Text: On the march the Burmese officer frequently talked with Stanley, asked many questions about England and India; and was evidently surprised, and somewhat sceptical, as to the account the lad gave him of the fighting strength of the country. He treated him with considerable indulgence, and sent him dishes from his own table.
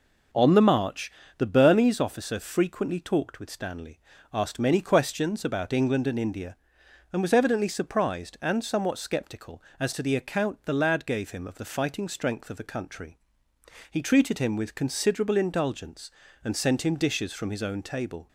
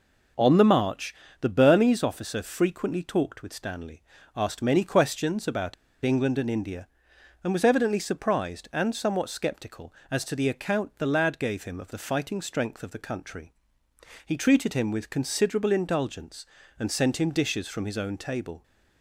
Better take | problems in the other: first | pauses between "march" and "the"; slight; at 1.1 s; 0.26 s long; slight in the first // pauses between "about" and "England"; slight; at 5.7 s; 0.30 s long

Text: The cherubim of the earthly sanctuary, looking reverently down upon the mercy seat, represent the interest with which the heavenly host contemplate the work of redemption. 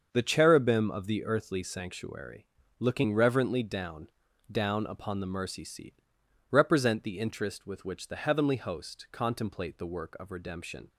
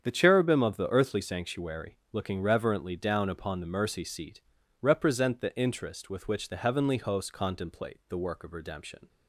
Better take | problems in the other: second | starts louder than the rest; until 1.1 s; 6.5 dB; strong in the second // says "down" twice; at 4.5 s

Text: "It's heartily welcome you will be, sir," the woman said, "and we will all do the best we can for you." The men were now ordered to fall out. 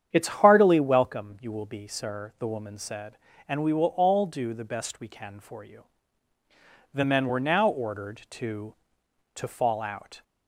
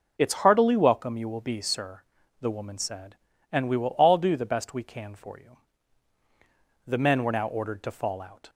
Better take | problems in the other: second | starts louder than the rest; strong; until 1.1 s; 8.5 dB // says "to" twice; at 9.3 s

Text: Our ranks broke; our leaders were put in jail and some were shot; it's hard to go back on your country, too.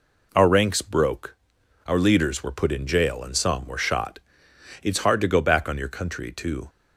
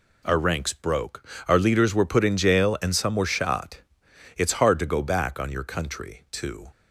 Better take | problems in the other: neither | none

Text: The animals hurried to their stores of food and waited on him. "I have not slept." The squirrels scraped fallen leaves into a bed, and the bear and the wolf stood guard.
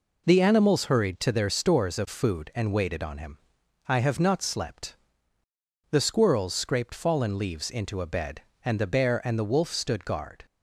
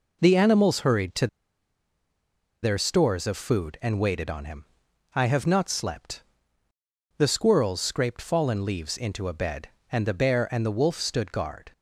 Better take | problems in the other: first | pauses between "to" and "their"; strong; at 1.2 s; 1.3 s long

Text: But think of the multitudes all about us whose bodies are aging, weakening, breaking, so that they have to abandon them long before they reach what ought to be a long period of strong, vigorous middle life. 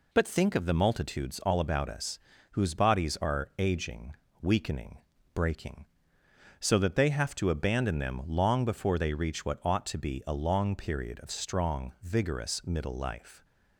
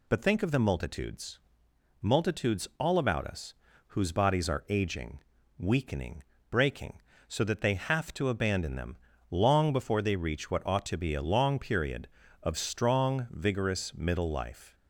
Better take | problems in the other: first | says "multitudes" twice; at 2.0 s // pauses between "us" and "whose"; slight; at 3.5 s; 0.34 s long; slight in the first // pauses between "them" and "long"; slight; at 8.9 s; 0.34 s long

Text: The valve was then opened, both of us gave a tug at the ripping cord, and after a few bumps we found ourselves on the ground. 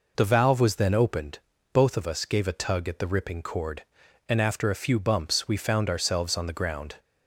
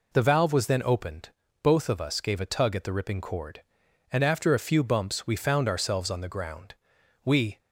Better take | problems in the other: first | goes on to say "We"; slight; from 7.2 s on; 0.34 s long

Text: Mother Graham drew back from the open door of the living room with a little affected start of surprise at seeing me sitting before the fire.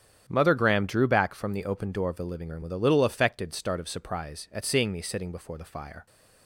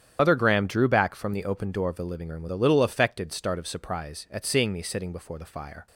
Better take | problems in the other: first | loses the start of "Mother"; at 0.1 s; 100 ms // starts louder than the rest; strong; until 1.2 s; 9.5 dB; strong in the first

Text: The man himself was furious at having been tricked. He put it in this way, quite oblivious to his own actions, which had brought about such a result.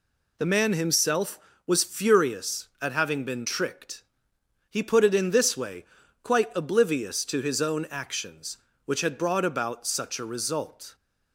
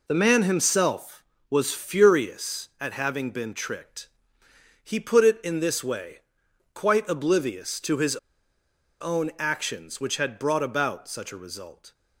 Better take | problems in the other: first | pauses between "his" and "own"; noticeable; at 8.1 s; 0.84 s long

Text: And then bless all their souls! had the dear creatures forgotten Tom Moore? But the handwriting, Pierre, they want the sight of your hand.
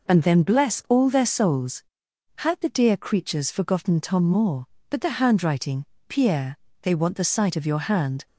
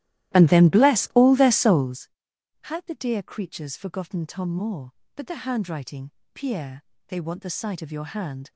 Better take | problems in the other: first | starts louder than the rest; strong; until 2.0 s; 14.5 dB

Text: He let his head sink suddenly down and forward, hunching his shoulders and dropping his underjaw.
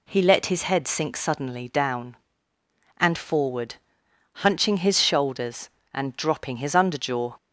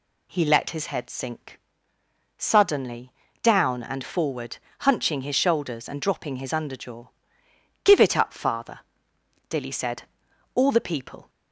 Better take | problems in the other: first | pauses between "sink" and "suddenly"; noticeable; at 1.5 s; 0.78 s long // pauses between "suddenly" and "down"; slight; at 3.1 s; 0.30 s long // goes on to say "Give it up father Dilly said All the people"; strong; from 7.8 s on; 3.4 s long

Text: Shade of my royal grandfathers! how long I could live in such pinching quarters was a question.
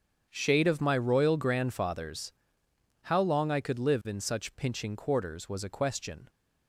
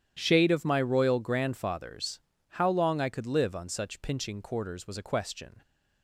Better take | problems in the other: first | starts louder than the rest; strong; until 1.2 s; 10.5 dB; strong in the first // says "on" for "in"; at 3.5 s

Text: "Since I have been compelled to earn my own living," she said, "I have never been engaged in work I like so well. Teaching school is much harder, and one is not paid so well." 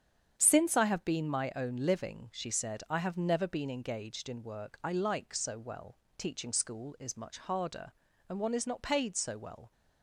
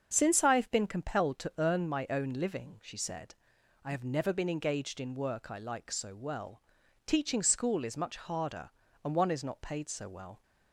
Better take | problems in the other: second | starts louder than the rest; strong; until 1.3 s; 8 dB; also in the second // skips "compelled to earn"; at 1.3 s

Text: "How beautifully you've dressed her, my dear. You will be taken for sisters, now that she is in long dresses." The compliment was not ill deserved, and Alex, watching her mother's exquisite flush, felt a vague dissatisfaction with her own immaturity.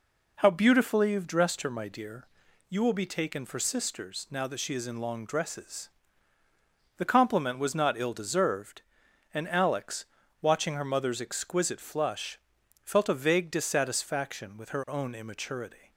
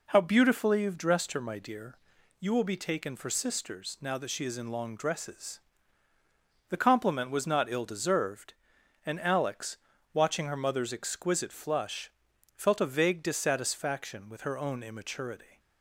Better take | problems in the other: neither | none

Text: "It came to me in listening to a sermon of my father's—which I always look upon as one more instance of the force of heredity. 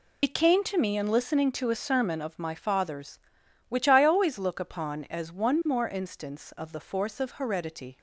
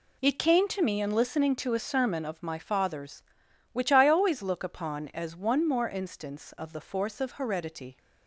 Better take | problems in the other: second | loses the start of "It"; at 0.2 s; 65 ms

